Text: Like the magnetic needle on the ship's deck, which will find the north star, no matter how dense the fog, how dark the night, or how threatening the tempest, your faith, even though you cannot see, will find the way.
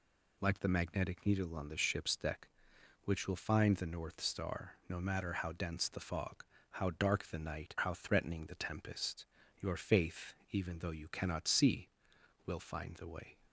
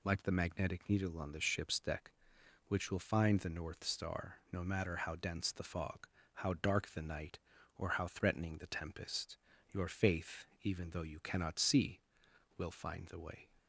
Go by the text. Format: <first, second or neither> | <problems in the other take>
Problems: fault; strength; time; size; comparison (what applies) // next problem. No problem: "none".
second | skips "or"; at 7.7 s